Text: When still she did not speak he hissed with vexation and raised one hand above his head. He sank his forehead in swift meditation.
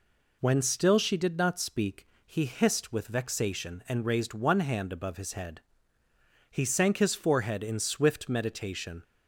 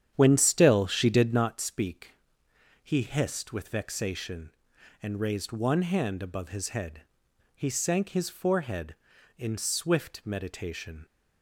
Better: first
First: pauses between "speak" and "he"; slight; at 2.0 s; 0.18 s long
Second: starts louder than the rest; strong; until 1.6 s; 9 dB // pauses between "speak" and "he"; noticeable; at 2.1 s; 0.74 s long

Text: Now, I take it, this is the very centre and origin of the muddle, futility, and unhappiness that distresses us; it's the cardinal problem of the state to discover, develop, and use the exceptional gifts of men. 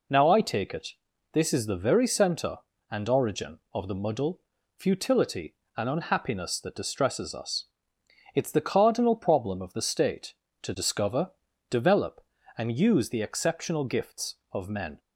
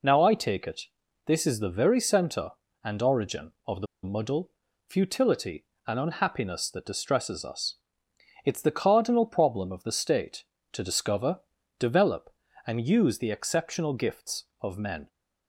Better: first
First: none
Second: pauses between "the" and "muddle"; slight; at 3.8 s; 0.17 s long

